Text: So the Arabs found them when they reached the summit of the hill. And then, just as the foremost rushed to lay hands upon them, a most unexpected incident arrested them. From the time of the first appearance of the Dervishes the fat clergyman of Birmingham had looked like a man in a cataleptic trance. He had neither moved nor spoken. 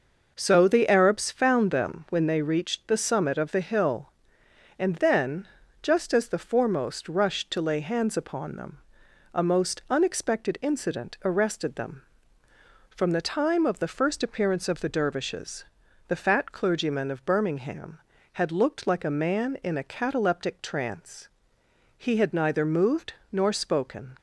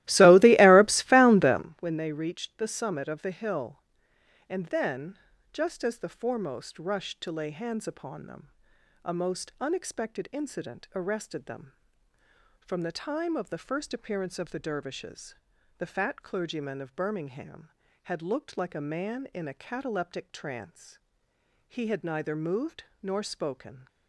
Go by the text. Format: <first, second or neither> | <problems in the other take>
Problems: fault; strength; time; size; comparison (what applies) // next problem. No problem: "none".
first | starts louder than the rest; strong; until 1.7 s; 17 dB // pauses between "Dervishes" and "the"; at 15.3 s; 0.42 s long; also in the first // pauses between "moved" and "nor"; slight; at 22.8 s; 0.18 s long; slight in the first